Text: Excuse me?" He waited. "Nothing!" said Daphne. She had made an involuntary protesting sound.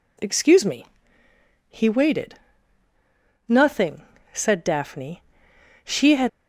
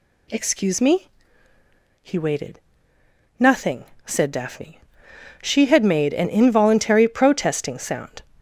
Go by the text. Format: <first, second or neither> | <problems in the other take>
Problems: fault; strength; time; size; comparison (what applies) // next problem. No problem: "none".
second | stops before "made an involuntary protesting sound"; at 6.2 s